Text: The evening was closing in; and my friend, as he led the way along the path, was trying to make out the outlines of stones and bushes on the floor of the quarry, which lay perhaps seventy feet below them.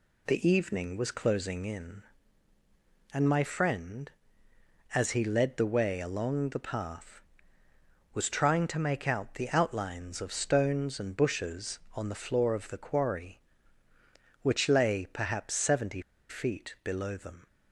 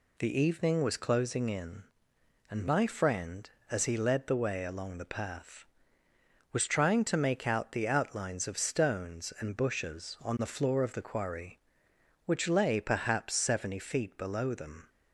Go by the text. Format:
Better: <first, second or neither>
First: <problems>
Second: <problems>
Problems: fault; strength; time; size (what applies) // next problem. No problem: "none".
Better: second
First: pauses between "seventy" and "feet"; slight; at 16.0 s; 0.28 s long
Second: none